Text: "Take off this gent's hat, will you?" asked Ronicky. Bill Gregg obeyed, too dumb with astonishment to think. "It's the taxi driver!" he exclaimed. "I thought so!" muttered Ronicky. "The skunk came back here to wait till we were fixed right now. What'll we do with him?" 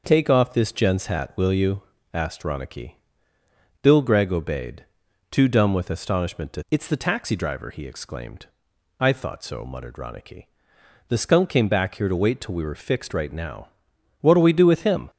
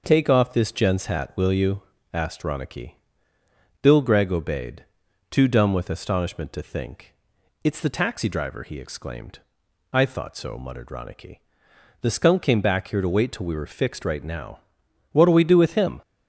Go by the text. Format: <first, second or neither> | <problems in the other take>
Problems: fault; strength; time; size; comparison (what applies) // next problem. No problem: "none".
second | skips "think"; at 6.6 s